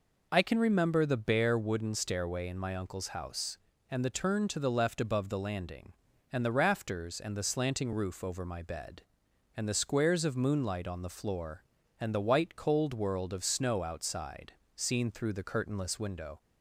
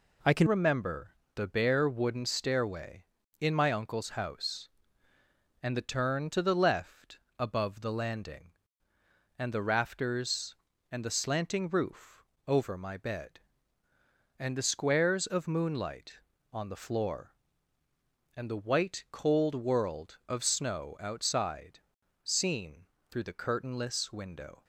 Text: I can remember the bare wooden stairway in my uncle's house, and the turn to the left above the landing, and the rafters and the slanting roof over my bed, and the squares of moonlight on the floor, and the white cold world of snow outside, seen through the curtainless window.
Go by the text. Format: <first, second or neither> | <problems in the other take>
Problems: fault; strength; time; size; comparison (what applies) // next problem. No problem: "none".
first | changes voice at "remember"; from 0.4 s on; 24.2 s long // pauses between "remember" and "the"; slight; at 1.1 s; 0.18 s long // pauses between "left" and "above"; slight; at 7.1 s; 0.20 s long // pauses between "roof" and "over"; slight; at 12.2 s; 0.22 s long // pauses between "seen" and "through"; slight; at 22.8 s; 0.24 s long